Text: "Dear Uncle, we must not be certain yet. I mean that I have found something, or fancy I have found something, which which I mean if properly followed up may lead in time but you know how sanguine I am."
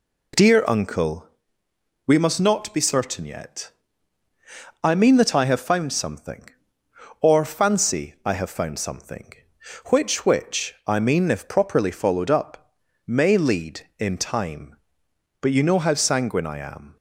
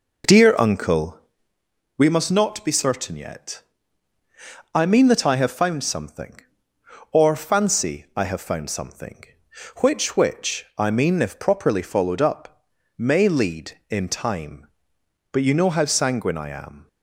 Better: first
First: pauses between "up" and "may"; slight; at 12.7 s; 0.34 s long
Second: starts louder than the rest; noticeable; until 1.7 s; 5 dB // pauses between "up" and "may"; slight; at 12.6 s; 0.34 s long

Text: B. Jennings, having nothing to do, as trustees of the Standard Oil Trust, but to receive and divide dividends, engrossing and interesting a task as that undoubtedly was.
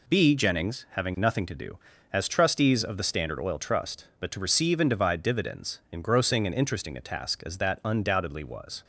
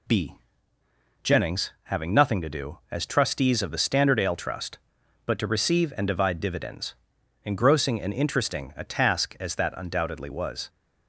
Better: first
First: none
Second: says "Ale" for "Oil"; at 4.2 s

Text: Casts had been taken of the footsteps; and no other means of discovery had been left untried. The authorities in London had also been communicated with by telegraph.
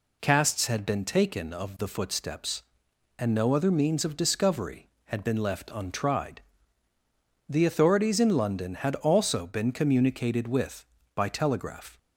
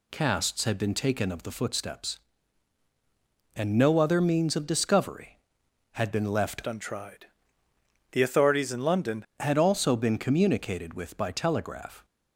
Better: first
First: none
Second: changes voice from "untried" to "London"; from 6.6 to 9.2 s; 2.6 s long

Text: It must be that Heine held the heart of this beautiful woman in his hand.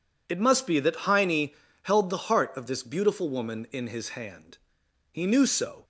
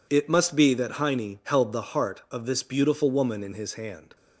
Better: second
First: pauses between "Heine" and "held"; slight; at 1.4 s; 0.32 s long // goes on to say "He knew so"; noticeable; from 5.1 s on; 0.72 s long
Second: none

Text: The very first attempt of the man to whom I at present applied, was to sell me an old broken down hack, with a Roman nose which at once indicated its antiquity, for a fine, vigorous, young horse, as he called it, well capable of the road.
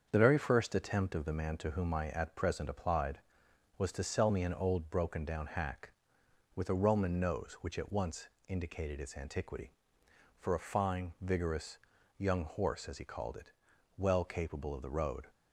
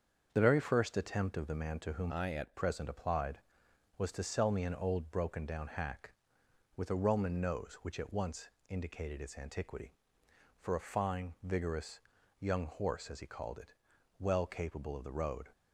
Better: first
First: starts louder than the rest; until 1.1 s; 7 dB // pauses between "once" and "indicated"; slight; at 8.2 s; 0.18 s long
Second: starts louder than the rest; until 1.3 s; 7 dB // changes voice from "I" to "at"; from 2.0 to 2.5 s; 0.5 s long // pauses between "once" and "indicated"; slight; at 8.4 s; 0.18 s long

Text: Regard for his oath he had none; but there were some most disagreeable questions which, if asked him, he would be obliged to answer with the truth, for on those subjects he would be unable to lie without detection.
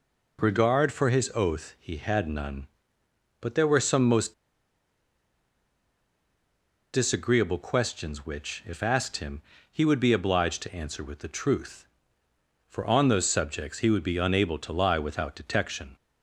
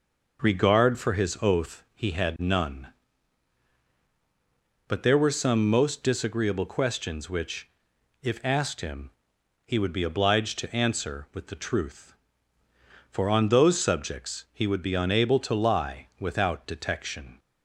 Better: second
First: pauses between "most" and "disagreeable"; strong; at 4.3 s; 2.6 s long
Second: none

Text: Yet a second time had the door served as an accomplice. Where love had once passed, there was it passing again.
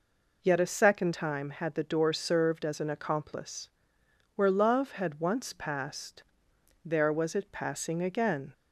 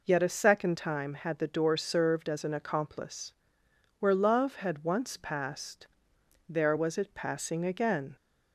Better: neither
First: none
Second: none

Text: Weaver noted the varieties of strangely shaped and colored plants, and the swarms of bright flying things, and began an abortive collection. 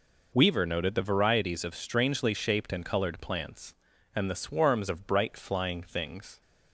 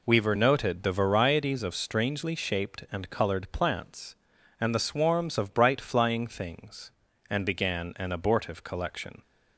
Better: second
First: stops before "and began an abortive collection"; at 6.4 s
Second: none

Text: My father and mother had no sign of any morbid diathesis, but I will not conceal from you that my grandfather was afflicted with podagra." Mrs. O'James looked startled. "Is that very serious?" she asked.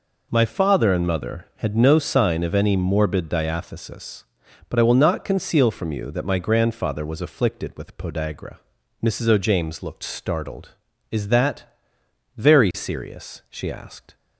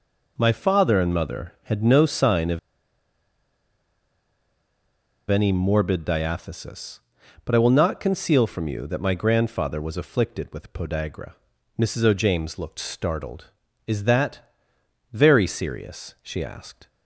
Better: first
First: pauses between "that" and "very"; noticeable; at 11.6 s; 0.72 s long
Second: pauses between "of" and "any"; strong; at 2.5 s; 2.7 s long // pauses between "that" and "very"; noticeable; at 14.3 s; 0.72 s long

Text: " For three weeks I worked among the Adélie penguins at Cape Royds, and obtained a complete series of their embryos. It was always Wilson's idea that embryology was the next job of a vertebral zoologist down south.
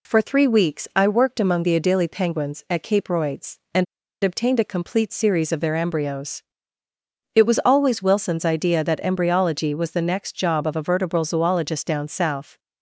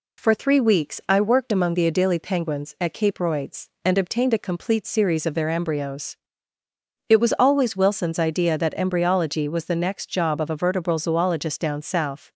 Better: second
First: pauses between "and" and "obtained"; at 3.8 s; 0.39 s long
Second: none

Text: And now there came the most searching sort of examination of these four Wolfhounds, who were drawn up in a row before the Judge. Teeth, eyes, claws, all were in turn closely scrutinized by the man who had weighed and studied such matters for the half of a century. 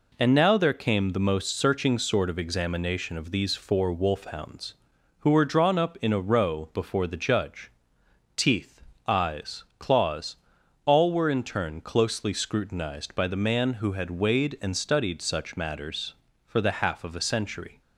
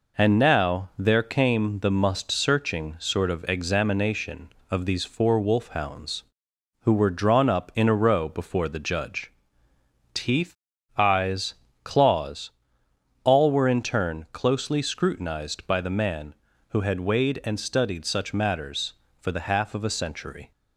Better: first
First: none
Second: says "must" for "most"; at 1.9 s

